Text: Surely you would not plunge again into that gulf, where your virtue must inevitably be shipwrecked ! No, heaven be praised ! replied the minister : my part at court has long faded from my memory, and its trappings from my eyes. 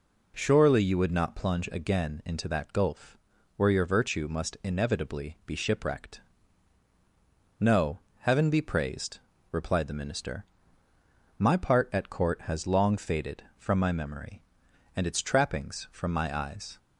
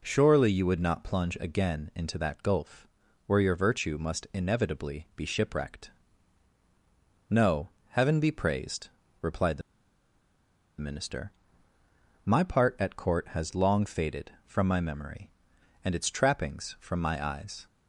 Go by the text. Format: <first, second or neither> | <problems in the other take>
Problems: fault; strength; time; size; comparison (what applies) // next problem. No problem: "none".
first | pauses between "the" and "minister"; at 9.6 s; 1.1 s long